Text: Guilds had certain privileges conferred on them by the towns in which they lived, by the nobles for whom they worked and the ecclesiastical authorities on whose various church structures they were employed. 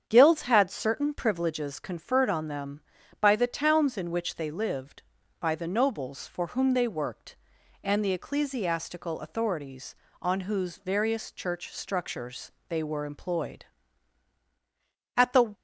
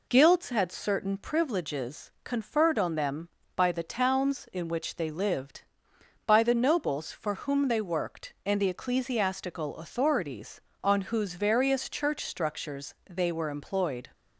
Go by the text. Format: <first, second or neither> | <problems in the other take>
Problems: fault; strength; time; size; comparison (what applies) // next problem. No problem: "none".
second | starts louder than the rest; strong; until 1.0 s; 8 dB // pauses between "structures" and "they"; slight; at 12.4 s; 0.20 s long; slight in the second // goes on to say "At the"; slight; from 15.1 s on; 0.38 s long